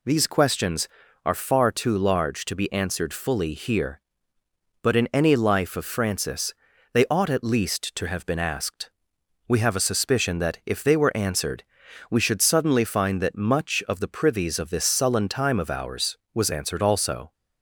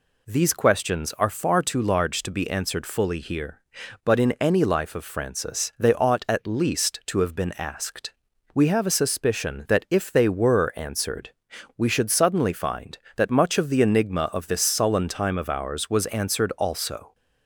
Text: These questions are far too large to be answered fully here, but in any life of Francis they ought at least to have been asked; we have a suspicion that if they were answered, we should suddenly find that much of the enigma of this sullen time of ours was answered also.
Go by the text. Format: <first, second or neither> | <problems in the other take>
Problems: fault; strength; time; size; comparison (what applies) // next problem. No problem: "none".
second | pauses between "Francis" and "they"; at 6.5 s; 0.38 s long // says "privies" for "enigma"; at 14.0 s